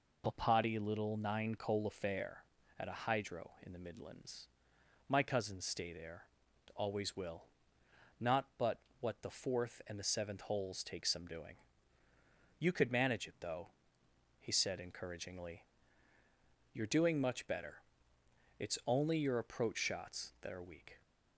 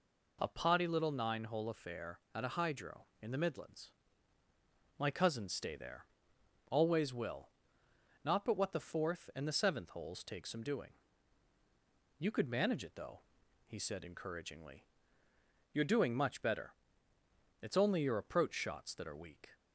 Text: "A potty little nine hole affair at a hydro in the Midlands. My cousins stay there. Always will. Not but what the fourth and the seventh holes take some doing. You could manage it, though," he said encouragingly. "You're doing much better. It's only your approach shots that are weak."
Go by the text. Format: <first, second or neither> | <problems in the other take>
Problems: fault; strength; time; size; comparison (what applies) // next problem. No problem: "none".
second | says "coal" for "hole"; at 1.5 s // pauses between "but" and "what"; slight; at 8.7 s; 0.22 s long